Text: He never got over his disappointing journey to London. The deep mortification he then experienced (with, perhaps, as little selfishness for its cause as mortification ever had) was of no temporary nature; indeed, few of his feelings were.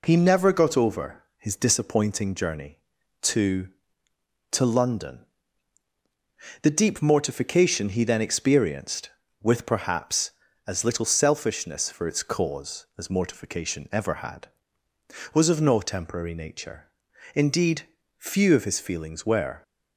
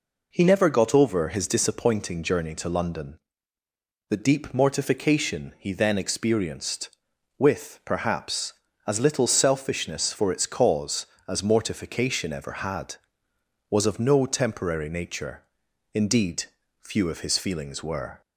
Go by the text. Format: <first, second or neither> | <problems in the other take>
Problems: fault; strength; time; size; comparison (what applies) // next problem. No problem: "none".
second | pauses between "over" and "his"; slight; at 1.2 s; 0.16 s long // says "to" twice; at 4.5 s